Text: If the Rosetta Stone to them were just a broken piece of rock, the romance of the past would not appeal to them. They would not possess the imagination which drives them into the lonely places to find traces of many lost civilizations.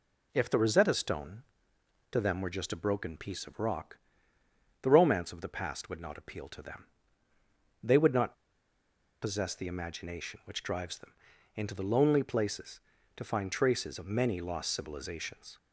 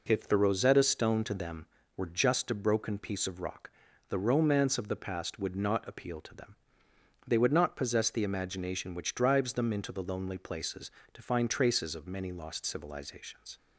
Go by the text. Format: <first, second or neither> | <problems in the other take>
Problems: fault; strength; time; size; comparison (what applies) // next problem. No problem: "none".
second | pauses between "not" and "possess"; noticeable; at 8.3 s; 0.87 s long // pauses between "them" and "into"; at 11.1 s; 0.42 s long